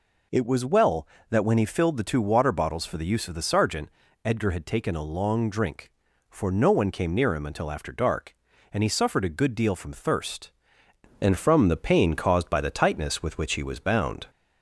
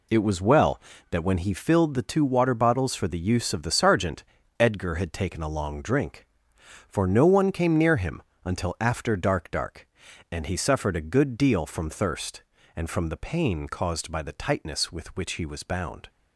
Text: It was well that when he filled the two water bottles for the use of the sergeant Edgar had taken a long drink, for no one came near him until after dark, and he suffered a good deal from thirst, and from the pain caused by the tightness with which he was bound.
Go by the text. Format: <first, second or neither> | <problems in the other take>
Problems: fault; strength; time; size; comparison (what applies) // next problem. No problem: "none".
first | pauses between "sergeant" and "Edgar"; slight; at 4.2 s; 0.36 s long; slight in the first // pauses between "him" and "until"; slight; at 8.2 s; 0.20 s long // says "dark" twice; at 9.5 s